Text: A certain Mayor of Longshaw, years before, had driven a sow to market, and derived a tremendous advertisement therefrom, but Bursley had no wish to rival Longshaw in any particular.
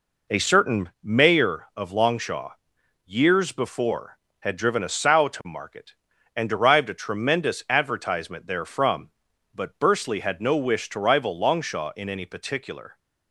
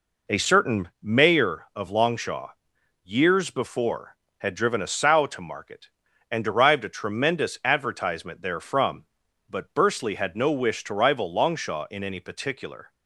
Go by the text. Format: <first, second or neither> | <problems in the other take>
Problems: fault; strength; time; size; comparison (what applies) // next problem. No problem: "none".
neither | none